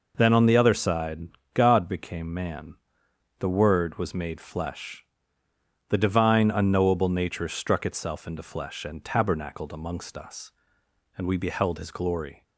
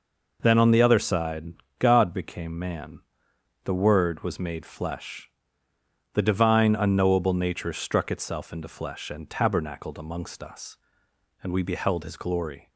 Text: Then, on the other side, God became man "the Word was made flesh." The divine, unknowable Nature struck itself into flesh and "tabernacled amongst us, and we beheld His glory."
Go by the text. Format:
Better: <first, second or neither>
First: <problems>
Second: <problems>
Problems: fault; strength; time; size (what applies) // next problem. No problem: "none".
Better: neither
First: pauses between "man" and "the"; noticeable; at 2.7 s; 0.64 s long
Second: pauses between "man" and "the"; noticeable; at 3.0 s; 0.64 s long